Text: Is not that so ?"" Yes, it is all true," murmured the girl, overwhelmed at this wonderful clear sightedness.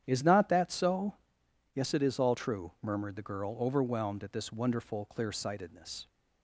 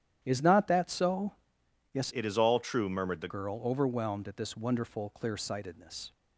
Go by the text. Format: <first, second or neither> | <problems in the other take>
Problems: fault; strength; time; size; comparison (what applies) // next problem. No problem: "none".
first | starts louder than the rest; strong; until 1.2 s; 9.5 dB; strong in the first // changes voice from "it" to "the"; from 2.1 to 3.2 s; 1.1 s long